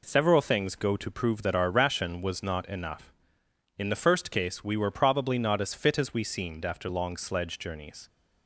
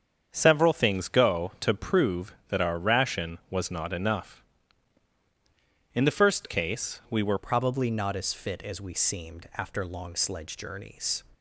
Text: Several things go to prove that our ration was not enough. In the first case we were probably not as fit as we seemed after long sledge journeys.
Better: first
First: none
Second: starts louder than the rest; strong; until 1.3 s; 7.5 dB // changes voice at "probably"; from 7.3 s on; 3.9 s long

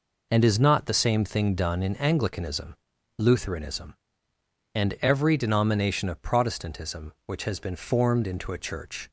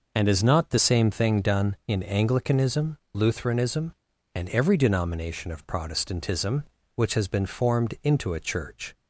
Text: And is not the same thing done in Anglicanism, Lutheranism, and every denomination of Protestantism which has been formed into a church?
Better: neither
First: none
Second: none

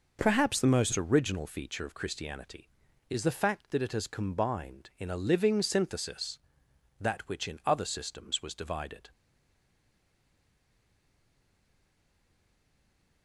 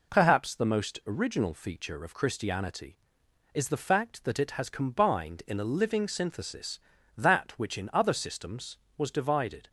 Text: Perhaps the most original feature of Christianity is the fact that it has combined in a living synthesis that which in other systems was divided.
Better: second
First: stays silent after the last word; strong; from 9.1 s on; 4.1 s long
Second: none

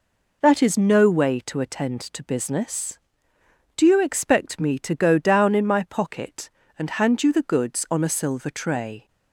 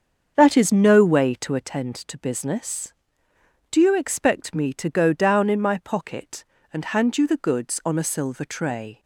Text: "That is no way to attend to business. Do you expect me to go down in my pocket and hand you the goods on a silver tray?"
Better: first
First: none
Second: starts louder than the rest; until 1.7 s; 7 dB

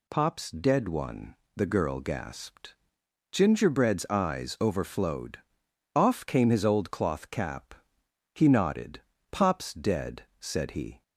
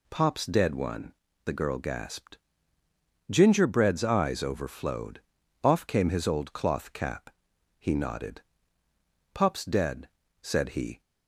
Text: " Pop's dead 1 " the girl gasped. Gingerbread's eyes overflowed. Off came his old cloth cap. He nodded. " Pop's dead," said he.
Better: neither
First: none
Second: none

